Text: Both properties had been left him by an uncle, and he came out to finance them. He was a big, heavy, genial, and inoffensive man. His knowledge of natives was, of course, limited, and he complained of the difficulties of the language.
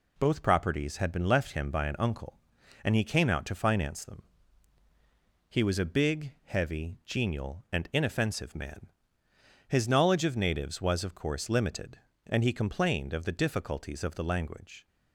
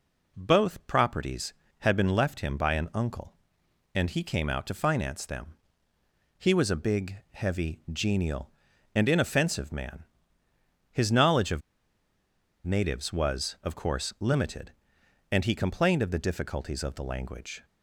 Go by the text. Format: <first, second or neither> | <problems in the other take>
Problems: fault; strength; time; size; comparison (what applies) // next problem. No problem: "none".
first | pauses between "of" and "natives"; at 11.6 s; 1.0 s long